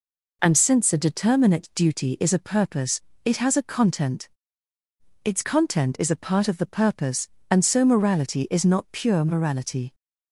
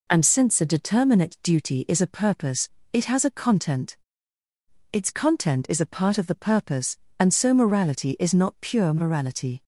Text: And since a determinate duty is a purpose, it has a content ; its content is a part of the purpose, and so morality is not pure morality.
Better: neither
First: none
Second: none

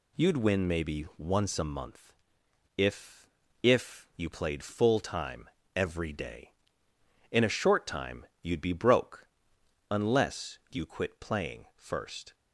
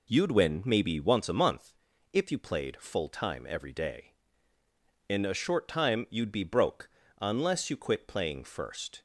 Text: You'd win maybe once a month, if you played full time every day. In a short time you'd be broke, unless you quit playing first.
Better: second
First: says "if" twice; at 3.6 s // pauses between "time" and "every"; slight; at 5.4 s; 0.26 s long // pauses between "time" and "you'd"; slight; at 8.2 s; 0.16 s long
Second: none

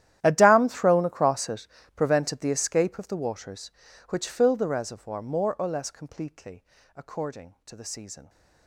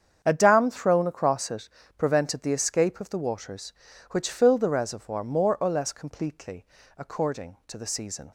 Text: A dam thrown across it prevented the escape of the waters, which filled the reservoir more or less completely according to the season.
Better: second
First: gets quieter; strong; throughout; 21 dB // starts louder than the rest; strong; until 1.2 s; 12 dB // pauses between "it" and "prevented"; slight; at 1.6 s; 0.30 s long // pauses between "completely" and "according"; slight; at 6.6 s; 0.32 s long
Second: starts louder than the rest; strong; until 1.2 s; 7.5 dB // pauses between "it" and "prevented"; slight; at 1.6 s; 0.30 s long // pauses between "completely" and "according"; slight; at 6.6 s; 0.32 s long

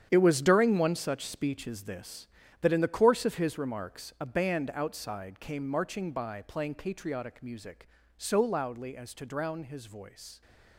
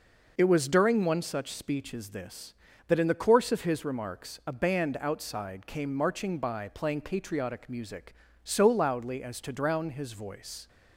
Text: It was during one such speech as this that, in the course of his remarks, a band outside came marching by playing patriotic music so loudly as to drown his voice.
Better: second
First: gets quieter; strong; throughout; 12 dB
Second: none

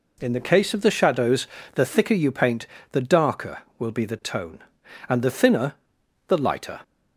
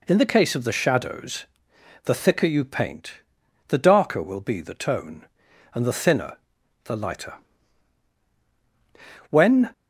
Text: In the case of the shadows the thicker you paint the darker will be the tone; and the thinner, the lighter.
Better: first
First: pauses between "shadows" and "the"; slight; at 1.4 s; 0.28 s long // pauses between "paint" and "the"; slight; at 2.6 s; 0.24 s long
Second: pauses between "shadows" and "the"; noticeable; at 1.4 s; 0.58 s long // pauses between "paint" and "the"; noticeable; at 3.2 s; 0.48 s long // goes on to say "When"; slight; from 9.2 s on; 0.42 s long

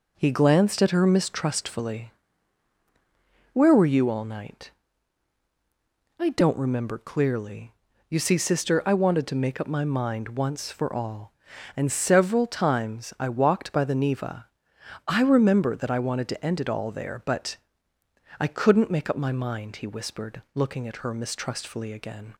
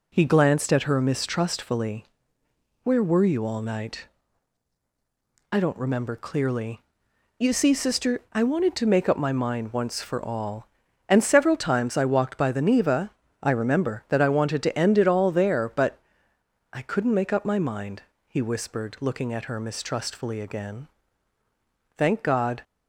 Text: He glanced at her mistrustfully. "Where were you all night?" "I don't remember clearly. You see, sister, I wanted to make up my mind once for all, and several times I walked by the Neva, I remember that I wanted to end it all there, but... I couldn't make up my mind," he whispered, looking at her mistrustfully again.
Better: first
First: none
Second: goes on to say "Thank God"; noticeable; from 21.9 s on; 0.64 s long

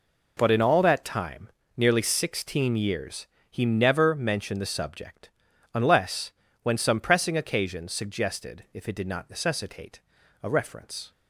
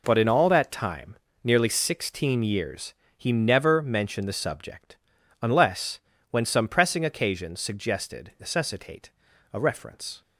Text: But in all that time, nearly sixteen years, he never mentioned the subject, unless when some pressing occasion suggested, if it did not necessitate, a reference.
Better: first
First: pauses between "unless" and "when"; slight; at 6.3 s; 0.30 s long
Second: pauses between "unless" and "when"; slight; at 5.9 s; 0.30 s long // skips "if it did not"; at 8.3 s

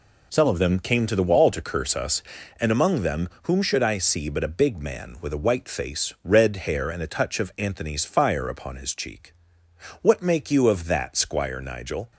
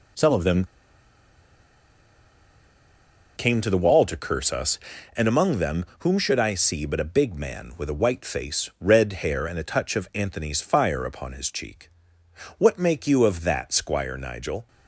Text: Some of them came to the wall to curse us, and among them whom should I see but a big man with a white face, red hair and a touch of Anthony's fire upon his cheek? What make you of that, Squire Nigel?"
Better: first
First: none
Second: pauses between "them" and "came"; strong; at 0.6 s; 2.7 s long

